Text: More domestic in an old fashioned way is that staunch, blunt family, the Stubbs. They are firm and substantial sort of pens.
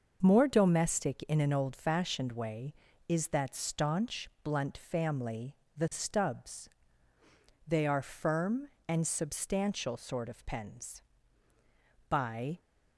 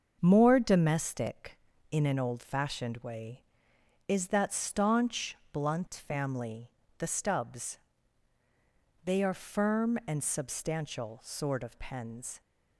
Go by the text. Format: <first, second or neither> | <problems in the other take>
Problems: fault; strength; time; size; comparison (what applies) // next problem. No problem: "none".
second | starts louder than the rest; noticeable; until 1.2 s; 6 dB; also in the second // goes on to say "By"; from 12.0 s on; 0.52 s long